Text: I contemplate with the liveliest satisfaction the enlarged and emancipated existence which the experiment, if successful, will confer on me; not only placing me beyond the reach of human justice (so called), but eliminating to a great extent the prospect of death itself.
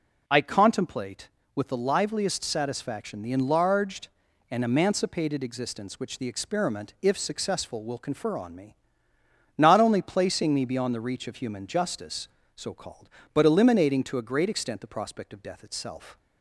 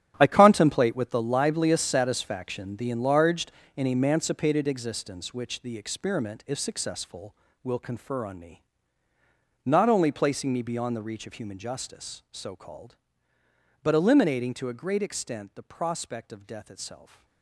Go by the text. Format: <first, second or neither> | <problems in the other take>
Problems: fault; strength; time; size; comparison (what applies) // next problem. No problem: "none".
first | gets quieter; strong; throughout; 13.5 dB